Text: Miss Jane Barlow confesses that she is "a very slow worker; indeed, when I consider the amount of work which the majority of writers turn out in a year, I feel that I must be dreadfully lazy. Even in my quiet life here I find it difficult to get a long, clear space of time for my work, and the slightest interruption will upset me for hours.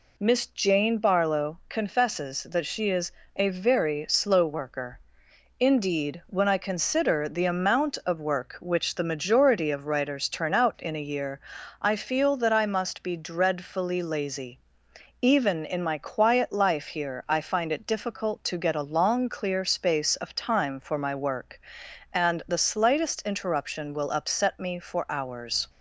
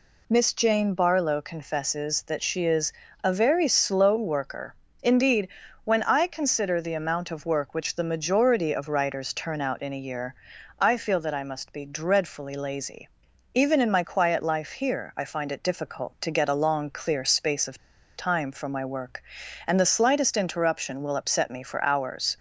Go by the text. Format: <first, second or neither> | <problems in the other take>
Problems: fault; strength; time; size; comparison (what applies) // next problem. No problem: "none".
first | pauses between "is" and "a"; slight; at 2.9 s; 0.32 s long; slight in the first // pauses between "of" and "time"; at 17.7 s; 0.39 s long